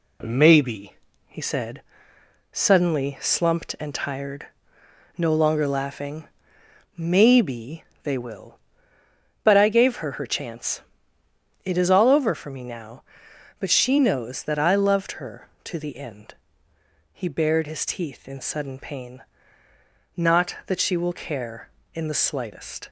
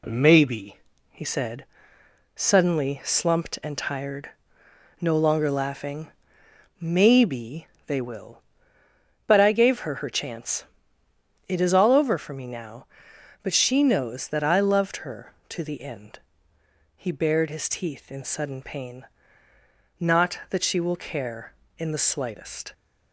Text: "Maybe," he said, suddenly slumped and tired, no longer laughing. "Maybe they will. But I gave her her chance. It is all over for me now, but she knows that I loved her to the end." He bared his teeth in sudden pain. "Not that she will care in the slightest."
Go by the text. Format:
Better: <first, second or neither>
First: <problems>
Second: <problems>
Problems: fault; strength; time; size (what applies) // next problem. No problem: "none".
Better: neither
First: pauses between "Maybe" and "they"; slight; at 7.8 s; 0.18 s long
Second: pauses between "Maybe" and "they"; slight; at 7.6 s; 0.18 s long